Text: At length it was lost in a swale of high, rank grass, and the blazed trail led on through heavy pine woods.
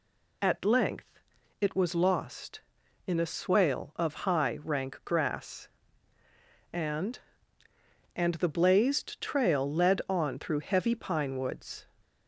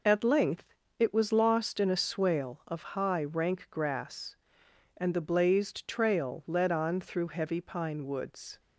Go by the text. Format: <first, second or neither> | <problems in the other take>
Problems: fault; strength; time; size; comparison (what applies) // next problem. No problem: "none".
second | pauses between "length" and "it"; at 1.1 s; 0.40 s long; slight in the second // says "and" twice; at 8.1 s